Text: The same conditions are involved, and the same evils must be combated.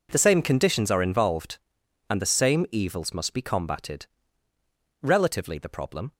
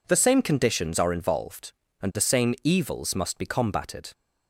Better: second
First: goes on to say "Relatively the problem"; noticeable; from 5.0 s on; 1.1 s long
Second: none

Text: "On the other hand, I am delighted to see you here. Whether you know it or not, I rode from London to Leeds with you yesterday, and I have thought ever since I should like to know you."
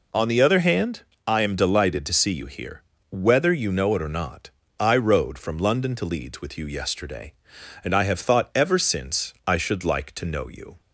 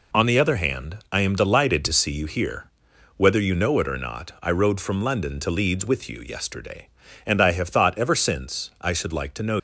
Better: first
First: none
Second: stops before "you"; at 9.5 s

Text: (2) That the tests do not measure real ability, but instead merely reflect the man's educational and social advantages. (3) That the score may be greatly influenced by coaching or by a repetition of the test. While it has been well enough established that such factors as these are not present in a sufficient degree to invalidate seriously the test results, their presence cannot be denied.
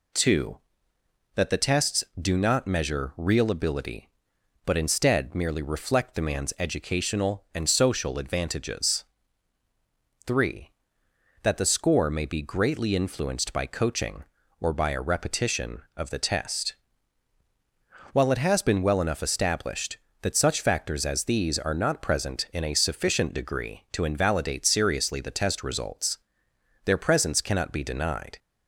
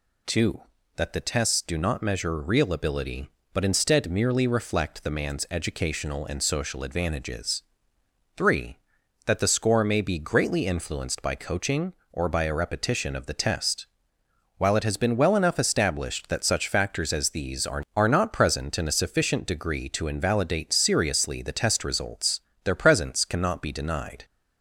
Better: first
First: none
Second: says "are" twice; at 17.9 s

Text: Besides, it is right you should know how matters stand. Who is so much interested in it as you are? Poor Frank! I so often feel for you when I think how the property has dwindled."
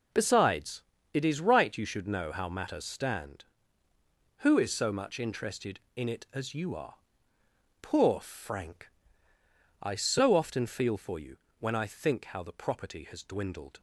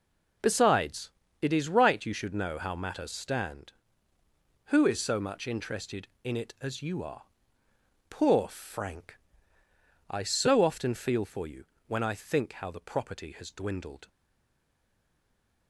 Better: first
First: pauses between "you" and "when"; slight; at 11.3 s; 0.24 s long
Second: pauses between "you" and "when"; slight; at 11.6 s; 0.24 s long // stays silent after the last word; noticeable; from 14.0 s on; 1.6 s long

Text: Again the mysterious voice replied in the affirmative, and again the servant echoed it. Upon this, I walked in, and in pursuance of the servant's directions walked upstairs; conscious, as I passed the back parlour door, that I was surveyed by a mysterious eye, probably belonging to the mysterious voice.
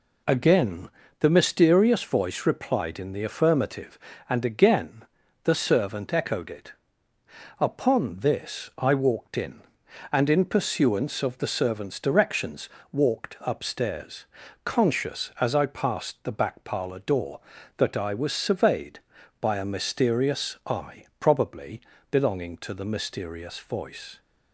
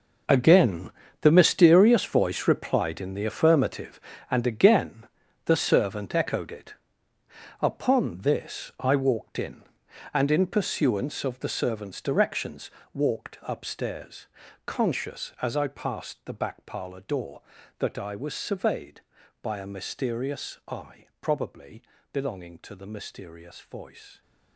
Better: first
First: pauses between "Again" and "the"; slight; at 0.8 s; 0.32 s long // pauses between "again" and "the"; at 5.0 s; 0.40 s long // pauses between "directions" and "walked"; slight; at 12.6 s; 0.20 s long // pauses between "probably" and "belonging"; slight; at 21.8 s; 0.30 s long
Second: gets quieter; strong; throughout; 13.5 dB // pauses between "Again" and "the"; slight; at 0.8 s; 0.32 s long // pauses between "again" and "the"; at 5.0 s; 0.40 s long // pauses between "directions" and "walked"; slight; at 12.7 s; 0.20 s long // pauses between "probably" and "belonging"; slight; at 21.8 s; 0.30 s long

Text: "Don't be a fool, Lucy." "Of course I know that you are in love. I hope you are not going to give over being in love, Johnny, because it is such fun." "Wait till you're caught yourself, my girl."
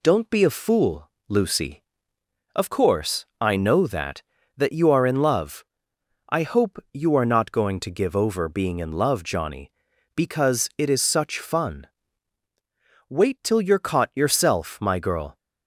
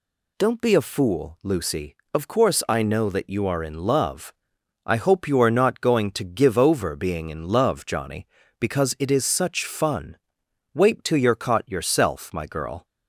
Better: second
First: says "that" twice; at 4.5 s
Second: none

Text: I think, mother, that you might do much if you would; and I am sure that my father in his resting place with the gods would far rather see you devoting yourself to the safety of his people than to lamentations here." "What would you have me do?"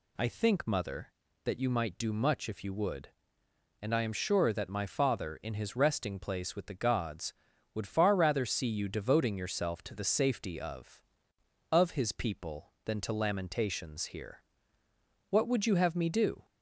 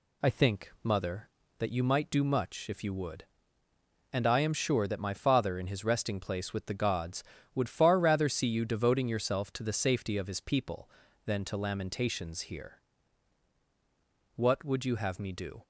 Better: second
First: says "of" twice; at 11.6 s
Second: none

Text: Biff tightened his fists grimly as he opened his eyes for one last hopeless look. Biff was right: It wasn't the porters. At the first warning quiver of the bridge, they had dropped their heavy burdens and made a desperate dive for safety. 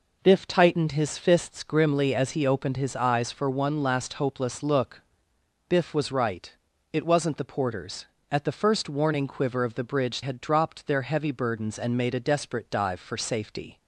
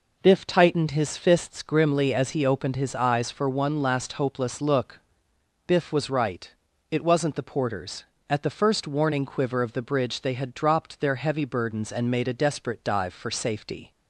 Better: second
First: skips "they"; at 10.2 s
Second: none

